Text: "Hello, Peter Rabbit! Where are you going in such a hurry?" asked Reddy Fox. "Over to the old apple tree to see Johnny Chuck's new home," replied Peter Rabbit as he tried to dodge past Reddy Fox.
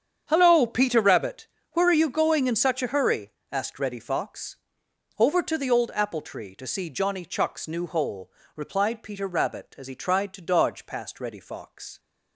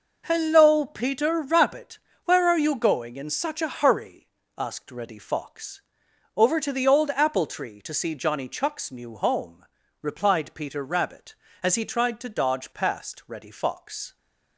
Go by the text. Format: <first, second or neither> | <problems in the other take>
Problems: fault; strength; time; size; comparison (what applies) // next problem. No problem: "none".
second | starts louder than the rest; strong; until 1.2 s; 8 dB // says "hole" for "home"; at 7.8 s